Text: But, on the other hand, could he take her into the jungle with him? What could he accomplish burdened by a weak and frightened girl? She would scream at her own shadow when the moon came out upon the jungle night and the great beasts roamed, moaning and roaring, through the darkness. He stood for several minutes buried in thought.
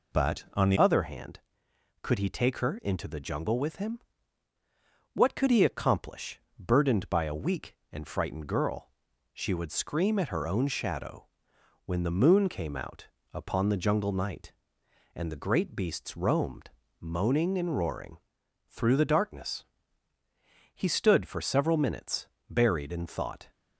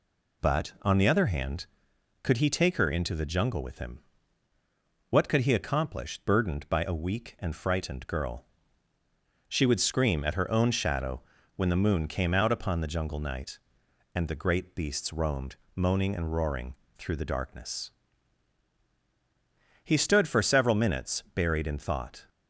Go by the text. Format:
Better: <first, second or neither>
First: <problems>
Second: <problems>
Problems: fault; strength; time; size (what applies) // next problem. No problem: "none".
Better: second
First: changes voice at "other"; from 0.7 s on; 22.8 s long // pauses between "accomplish" and "burdened"; slight; at 6.3 s; 0.20 s long // pauses between "shadow" and "when"; noticeable; at 11.2 s; 0.58 s long // pauses between "out" and "upon"; slight; at 13.0 s; 0.24 s long // pauses between "minutes" and "buried"; slight; at 22.2 s; 0.20 s long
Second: pauses between "shadow" and "when"; slight; at 11.2 s; 0.34 s long